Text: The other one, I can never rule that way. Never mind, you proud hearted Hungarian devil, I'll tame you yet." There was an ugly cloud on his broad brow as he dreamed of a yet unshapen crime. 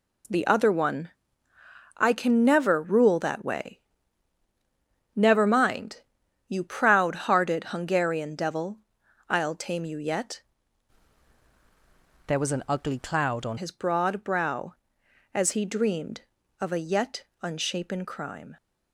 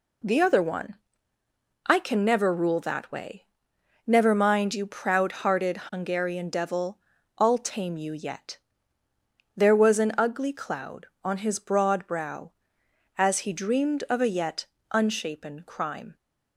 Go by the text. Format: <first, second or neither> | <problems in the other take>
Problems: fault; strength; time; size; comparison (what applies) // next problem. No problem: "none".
second | changes voice from "There" to "on"; from 12.2 to 13.5 s; 1.3 s long // pauses between "yet" and "unshapen"; slight; at 17.2 s; 0.16 s long; slight in the second